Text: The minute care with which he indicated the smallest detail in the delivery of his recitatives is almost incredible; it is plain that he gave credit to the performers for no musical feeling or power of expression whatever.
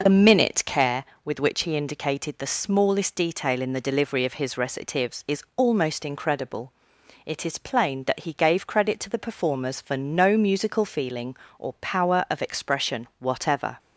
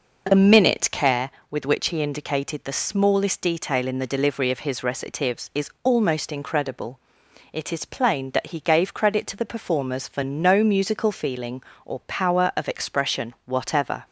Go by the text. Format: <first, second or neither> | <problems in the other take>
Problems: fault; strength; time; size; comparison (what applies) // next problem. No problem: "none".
neither | none